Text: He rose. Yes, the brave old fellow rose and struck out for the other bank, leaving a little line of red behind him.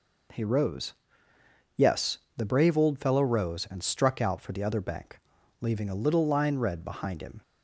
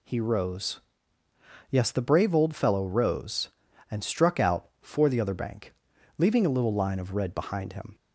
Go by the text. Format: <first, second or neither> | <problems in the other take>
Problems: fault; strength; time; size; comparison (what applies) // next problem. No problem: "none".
second | skips "of"; at 6.5 s